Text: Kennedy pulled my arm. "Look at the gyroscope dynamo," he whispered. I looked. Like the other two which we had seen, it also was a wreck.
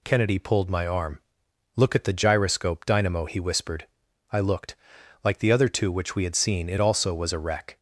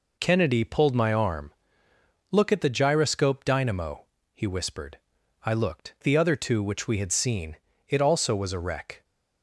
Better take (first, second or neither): first